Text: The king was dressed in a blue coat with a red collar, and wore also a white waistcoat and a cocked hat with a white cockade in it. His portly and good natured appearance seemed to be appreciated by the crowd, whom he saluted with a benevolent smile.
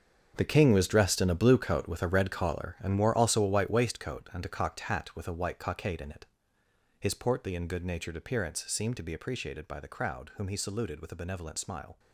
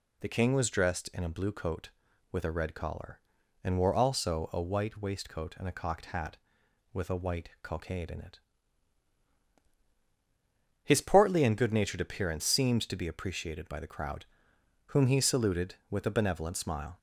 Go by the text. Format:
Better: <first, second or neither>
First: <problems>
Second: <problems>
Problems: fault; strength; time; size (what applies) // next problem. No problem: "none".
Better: second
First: gets quieter; strong; throughout; 13.5 dB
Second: none